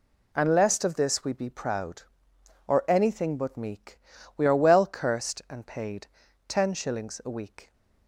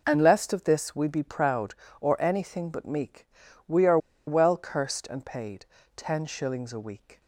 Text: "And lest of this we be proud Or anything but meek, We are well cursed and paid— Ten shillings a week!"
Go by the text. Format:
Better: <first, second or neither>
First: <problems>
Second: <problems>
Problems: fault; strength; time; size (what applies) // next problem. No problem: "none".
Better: first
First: none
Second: pauses between "are" and "well"; slight; at 3.9 s; 0.29 s long